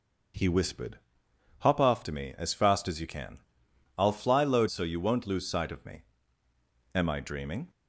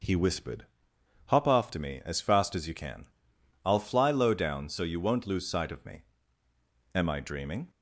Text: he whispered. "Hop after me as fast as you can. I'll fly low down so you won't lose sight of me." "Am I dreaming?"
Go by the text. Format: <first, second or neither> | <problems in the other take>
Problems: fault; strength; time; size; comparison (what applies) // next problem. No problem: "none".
second | starts louder than the rest; until 1.9 s; 6.5 dB; also in the second // skips "down"; at 4.6 s